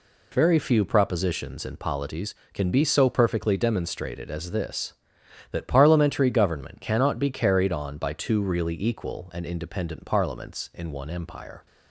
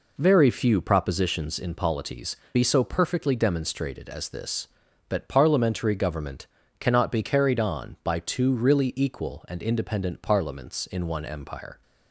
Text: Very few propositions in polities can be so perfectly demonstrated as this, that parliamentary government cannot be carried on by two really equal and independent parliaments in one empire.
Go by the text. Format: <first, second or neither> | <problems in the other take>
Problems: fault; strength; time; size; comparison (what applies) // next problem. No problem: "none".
first | skips "can"; at 2.4 s // pauses between "government" and "cannot"; slight; at 6.4 s; 0.32 s long